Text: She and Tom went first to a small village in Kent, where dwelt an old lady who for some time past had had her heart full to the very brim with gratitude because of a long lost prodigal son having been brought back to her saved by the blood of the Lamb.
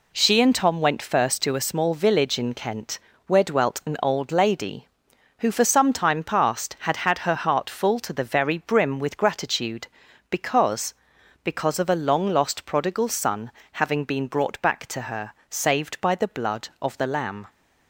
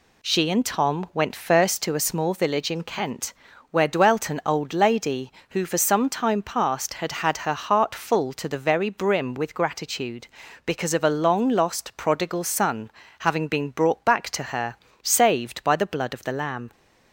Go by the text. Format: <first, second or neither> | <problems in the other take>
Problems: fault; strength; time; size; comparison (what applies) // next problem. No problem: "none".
second | says "because" twice; at 11.4 s // pauses between "son" and "having"; slight; at 13.5 s; 0.22 s long; slight in the second // pauses between "her" and "saved"; slight; at 15.3 s; 0.16 s long; slight in the second